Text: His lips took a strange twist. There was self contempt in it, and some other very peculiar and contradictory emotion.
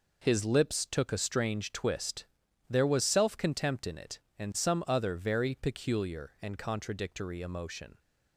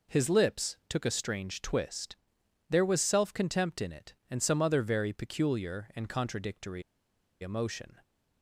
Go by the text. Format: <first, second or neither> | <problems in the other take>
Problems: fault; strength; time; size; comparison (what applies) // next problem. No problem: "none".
first | pauses between "contradictory" and "emotion"; noticeable; at 6.8 s; 0.59 s long